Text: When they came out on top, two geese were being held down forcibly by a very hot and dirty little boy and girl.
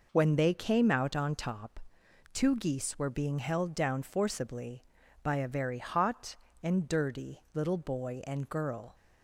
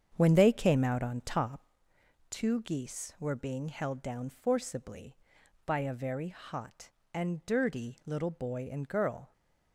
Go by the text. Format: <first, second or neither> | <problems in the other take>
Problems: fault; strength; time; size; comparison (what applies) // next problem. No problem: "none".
first | starts louder than the rest; strong; until 1.8 s; 8 dB